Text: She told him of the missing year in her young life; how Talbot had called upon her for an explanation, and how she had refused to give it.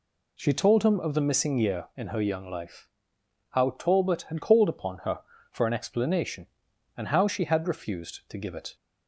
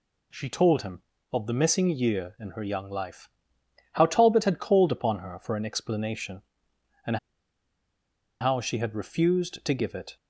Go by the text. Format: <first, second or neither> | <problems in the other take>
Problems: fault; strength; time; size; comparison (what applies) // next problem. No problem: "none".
first | pauses between "and" and "how"; at 7.1 s; 1.2 s long